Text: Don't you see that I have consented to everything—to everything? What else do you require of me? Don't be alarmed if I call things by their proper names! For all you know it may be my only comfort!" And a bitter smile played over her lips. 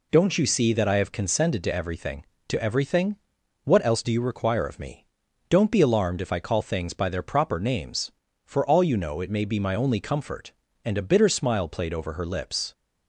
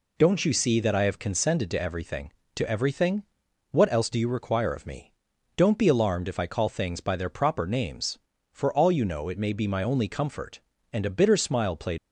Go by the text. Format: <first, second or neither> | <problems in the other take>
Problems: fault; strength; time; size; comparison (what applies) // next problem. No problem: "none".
first | stops before "over her lips"; at 11.9 s